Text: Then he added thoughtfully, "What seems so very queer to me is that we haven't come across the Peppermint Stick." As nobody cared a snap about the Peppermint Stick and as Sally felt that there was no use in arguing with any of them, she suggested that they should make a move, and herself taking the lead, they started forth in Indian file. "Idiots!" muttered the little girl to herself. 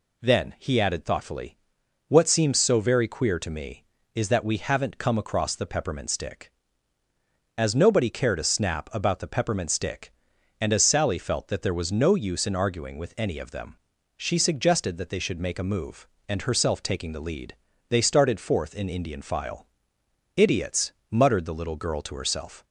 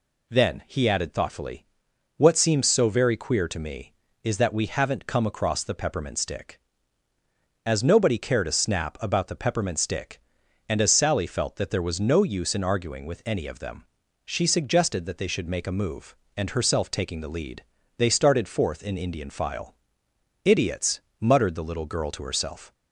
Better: neither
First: none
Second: none

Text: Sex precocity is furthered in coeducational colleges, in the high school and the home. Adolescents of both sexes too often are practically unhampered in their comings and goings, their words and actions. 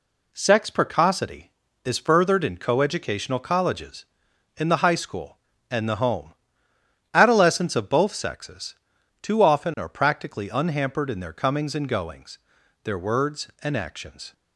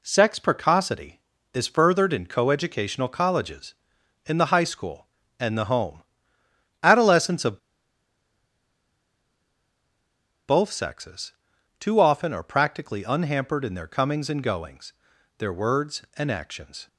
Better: first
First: pauses between "sexes" and "too"; noticeable; at 8.7 s; 0.46 s long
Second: pauses between "of" and "both"; strong; at 7.5 s; 2.8 s long // pauses between "sexes" and "too"; noticeable; at 11.3 s; 0.46 s long

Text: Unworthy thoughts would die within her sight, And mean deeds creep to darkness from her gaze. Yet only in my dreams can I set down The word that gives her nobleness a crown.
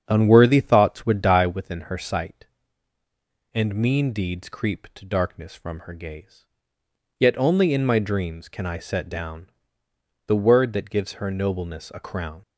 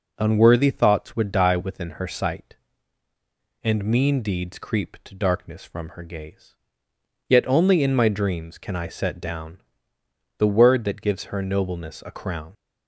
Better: second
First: starts louder than the rest; strong; until 1.6 s; 7.5 dB // pauses between "down" and "The"; noticeable; at 9.4 s; 0.76 s long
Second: pauses between "down" and "The"; noticeable; at 9.6 s; 0.76 s long

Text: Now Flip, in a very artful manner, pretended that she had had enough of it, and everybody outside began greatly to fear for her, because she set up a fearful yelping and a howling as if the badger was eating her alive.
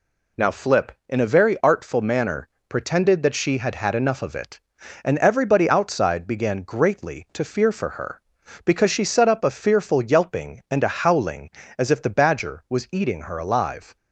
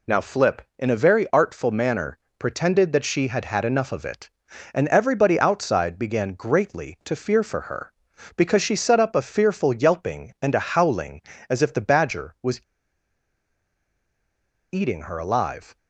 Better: first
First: none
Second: pauses between "was" and "eating"; strong; at 12.5 s; 2.1 s long

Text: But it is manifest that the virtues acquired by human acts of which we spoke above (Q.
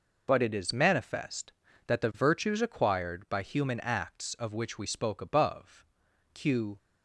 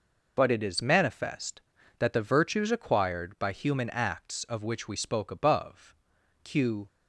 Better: neither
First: none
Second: none

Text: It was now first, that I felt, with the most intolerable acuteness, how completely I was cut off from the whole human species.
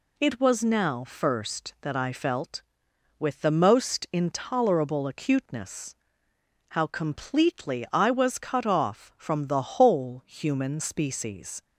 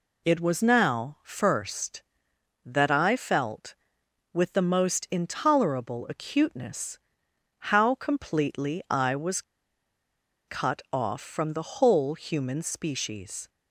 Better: first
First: none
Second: pauses between "was" and "cut"; at 9.4 s; 1.0 s long

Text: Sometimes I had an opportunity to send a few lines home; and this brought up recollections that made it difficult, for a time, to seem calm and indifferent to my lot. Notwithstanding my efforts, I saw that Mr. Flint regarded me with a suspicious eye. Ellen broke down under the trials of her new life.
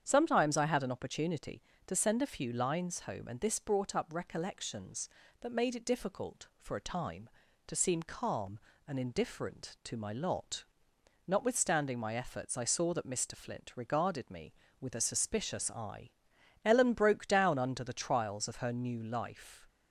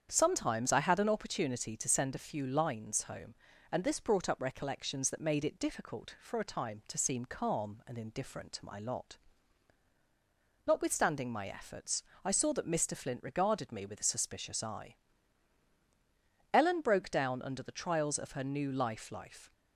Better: first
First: starts louder than the rest; strong; until 1.1 s; 8 dB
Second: starts louder than the rest; strong; until 1.1 s; 8 dB // says "life" twice; at 19.1 s

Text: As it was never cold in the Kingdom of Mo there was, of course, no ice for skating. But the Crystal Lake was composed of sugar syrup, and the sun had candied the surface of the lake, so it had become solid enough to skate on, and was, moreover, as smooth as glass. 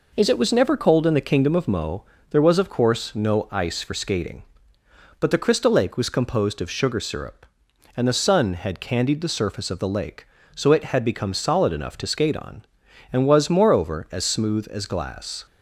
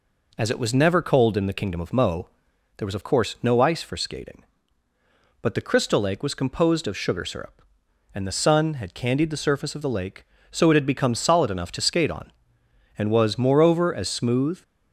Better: first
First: pauses between "Mo" and "there"; slight; at 2.0 s; 0.26 s long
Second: pauses between "Mo" and "there"; noticeable; at 2.2 s; 0.50 s long // stops before "as glass"; at 14.6 s

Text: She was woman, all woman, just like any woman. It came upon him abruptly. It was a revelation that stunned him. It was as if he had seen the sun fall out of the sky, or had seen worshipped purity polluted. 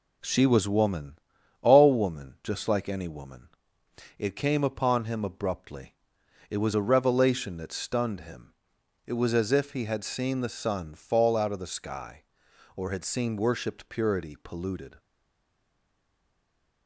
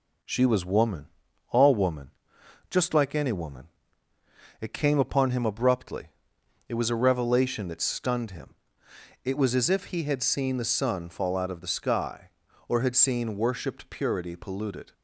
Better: second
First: stays silent after the last word; noticeable; from 14.9 s on; 1.9 s long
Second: none

